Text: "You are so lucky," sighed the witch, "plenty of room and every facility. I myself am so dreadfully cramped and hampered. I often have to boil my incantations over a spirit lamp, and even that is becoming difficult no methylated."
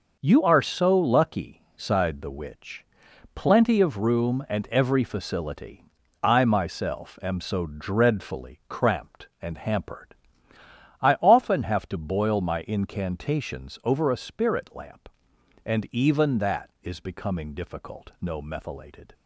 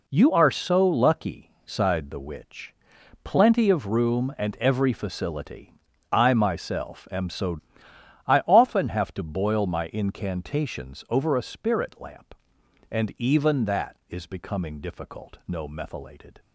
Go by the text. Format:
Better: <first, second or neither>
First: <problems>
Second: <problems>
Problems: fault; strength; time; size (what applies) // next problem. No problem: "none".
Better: first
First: none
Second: skips "dreadfully cramped and hampered"; at 7.9 s